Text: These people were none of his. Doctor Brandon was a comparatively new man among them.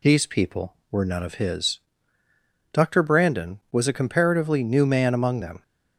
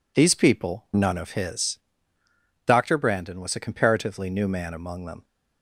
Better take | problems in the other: first | skips "were"; at 0.9 s

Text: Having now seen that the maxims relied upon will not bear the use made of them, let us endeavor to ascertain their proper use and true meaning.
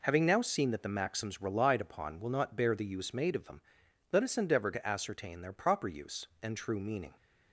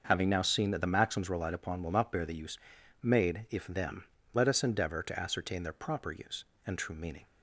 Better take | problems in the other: first | starts louder than the rest; until 1.0 s; 6.5 dB // pauses between "use" and "made"; at 2.5 s; 0.42 s long // says "if" for "of"; at 3.4 s

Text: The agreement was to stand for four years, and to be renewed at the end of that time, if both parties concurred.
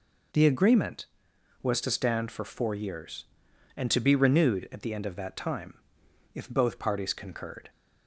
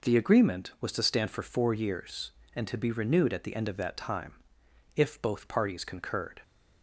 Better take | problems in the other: neither | none

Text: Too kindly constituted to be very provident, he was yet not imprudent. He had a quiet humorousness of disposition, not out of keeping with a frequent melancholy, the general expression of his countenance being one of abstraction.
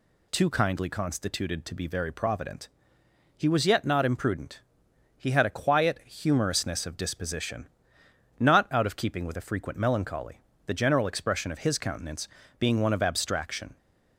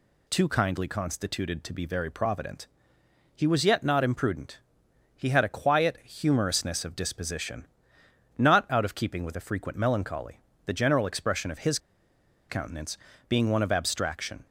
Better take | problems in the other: first | pauses between "his" and "countenance"; noticeable; at 11.7 s; 0.70 s long // pauses between "countenance" and "being"; slight; at 12.9 s; 0.32 s long; slight in the first

